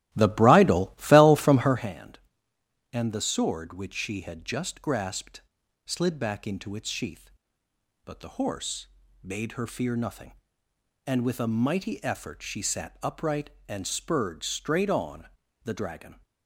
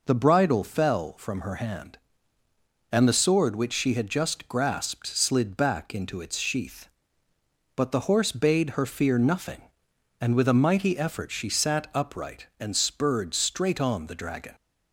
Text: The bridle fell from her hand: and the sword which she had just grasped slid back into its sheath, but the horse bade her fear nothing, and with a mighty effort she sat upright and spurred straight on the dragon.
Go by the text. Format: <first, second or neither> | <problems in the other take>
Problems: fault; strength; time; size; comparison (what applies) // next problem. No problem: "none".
second | starts louder than the rest; strong; until 1.9 s; 15 dB // pauses between "grasped" and "slid"; noticeable; at 5.3 s; 0.46 s long // pauses between "horse" and "bade"; at 8.8 s; 0.38 s long // pauses between "on" and "the"; slight; at 15.2 s; 0.36 s long